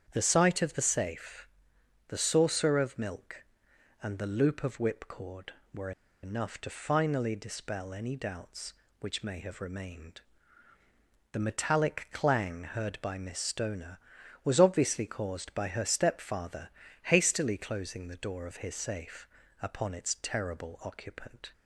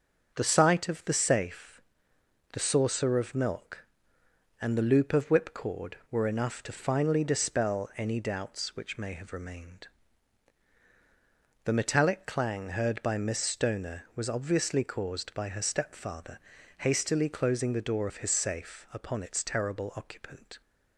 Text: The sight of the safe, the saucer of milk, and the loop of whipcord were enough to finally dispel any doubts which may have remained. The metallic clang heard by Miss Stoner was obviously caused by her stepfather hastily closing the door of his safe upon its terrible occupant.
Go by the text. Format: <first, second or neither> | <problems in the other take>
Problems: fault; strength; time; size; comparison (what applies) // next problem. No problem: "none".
second | starts louder than the rest; strong; until 1.1 s; 8.5 dB; also in the second // pauses between "were" and "enough"; slight; at 5.9 s; 0.32 s long // pauses between "stepfather" and "hastily"; slight; at 16.6 s; 0.36 s long; also in the second // pauses between "safe" and "upon"; slight; at 19.2 s; 0.36 s long